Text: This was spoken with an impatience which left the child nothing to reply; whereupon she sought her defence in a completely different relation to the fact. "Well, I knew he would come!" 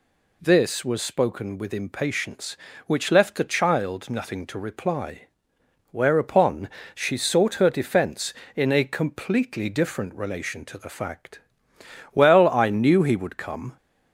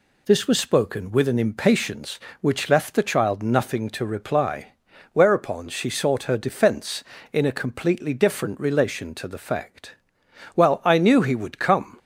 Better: second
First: skips "an"; at 1.7 s // pauses between "whereupon" and "she"; slight; at 6.7 s; 0.24 s long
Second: none

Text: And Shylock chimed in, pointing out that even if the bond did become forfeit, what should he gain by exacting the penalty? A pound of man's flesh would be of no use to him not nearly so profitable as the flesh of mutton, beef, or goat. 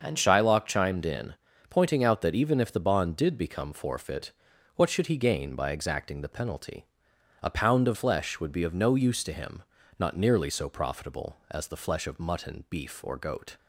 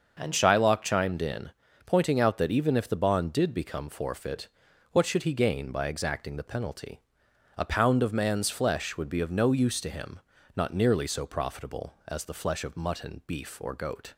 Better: second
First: starts louder than the rest; until 1.0 s; 6.5 dB // skips "man's"; at 7.9 s // pauses between "him" and "not"; slight; at 9.6 s; 0.36 s long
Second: starts louder than the rest; until 1.1 s; 6.5 dB // pauses between "him" and "not"; slight; at 10.2 s; 0.36 s long

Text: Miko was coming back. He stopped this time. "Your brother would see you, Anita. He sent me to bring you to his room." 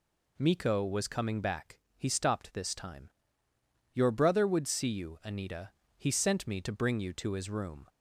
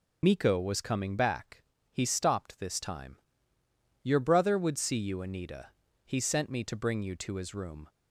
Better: first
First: none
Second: loses the start of "Miko"; at 0.2 s; 65 ms

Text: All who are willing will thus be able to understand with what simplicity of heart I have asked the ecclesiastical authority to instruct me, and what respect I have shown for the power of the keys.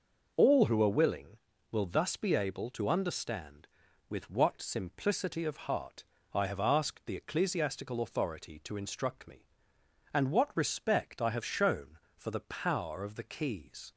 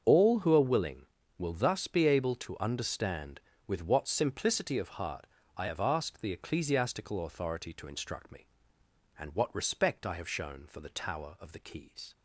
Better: first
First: pauses between "heart" and "I"; slight; at 6.0 s; 0.28 s long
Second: starts louder than the rest; until 1.0 s; 7 dB // pauses between "heart" and "I"; slight; at 5.2 s; 0.30 s long // says "tower" for "power"; at 10.9 s

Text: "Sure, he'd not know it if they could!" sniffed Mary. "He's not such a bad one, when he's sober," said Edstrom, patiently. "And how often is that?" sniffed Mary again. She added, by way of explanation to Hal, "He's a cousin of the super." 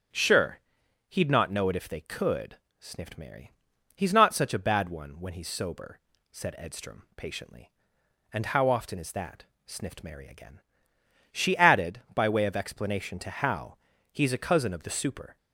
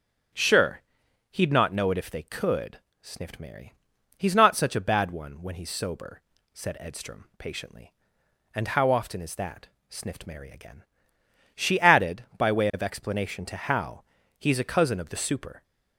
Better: neither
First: starts louder than the rest; strong; until 1.6 s; 8.5 dB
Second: starts louder than the rest; strong; until 1.8 s; 8.5 dB

